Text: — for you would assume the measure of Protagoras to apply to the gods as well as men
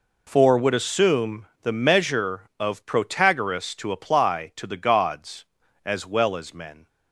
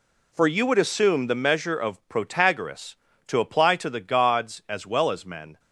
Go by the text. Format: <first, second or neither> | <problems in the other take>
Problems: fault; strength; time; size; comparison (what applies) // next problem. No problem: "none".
second | skips "you"; at 0.5 s // pauses between "assume" and "the"; slight; at 1.4 s; 0.16 s long